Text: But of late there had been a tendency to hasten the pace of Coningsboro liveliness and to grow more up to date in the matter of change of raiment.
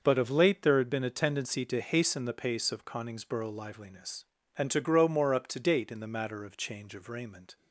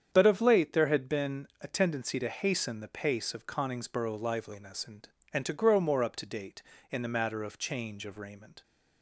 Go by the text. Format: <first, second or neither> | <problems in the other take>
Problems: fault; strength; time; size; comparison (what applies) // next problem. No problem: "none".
first | starts louder than the rest; strong; until 1.1 s; 8 dB; noticeable in the first // pauses between "been" and "a"; slight; at 1.4 s; 0.16 s long // says "and" twice; at 5.3 s